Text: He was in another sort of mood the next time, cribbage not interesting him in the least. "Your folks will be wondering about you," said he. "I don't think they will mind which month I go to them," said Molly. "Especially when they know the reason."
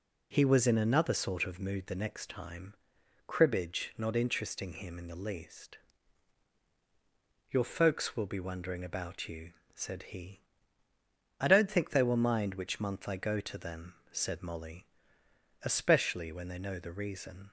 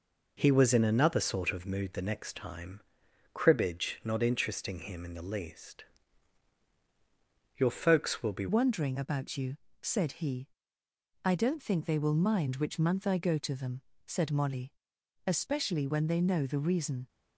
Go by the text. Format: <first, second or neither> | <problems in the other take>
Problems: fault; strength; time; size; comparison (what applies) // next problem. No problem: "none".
first | changes voice at "wondering"; from 8.4 s on; 8.6 s long